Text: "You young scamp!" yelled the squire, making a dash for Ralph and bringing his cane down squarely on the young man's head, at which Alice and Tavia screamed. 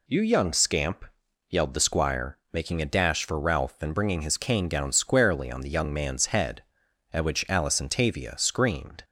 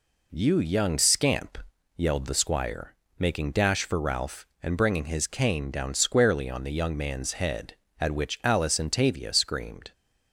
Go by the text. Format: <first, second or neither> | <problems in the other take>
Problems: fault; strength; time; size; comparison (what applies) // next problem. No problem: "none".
first | skips "a"; at 3.5 s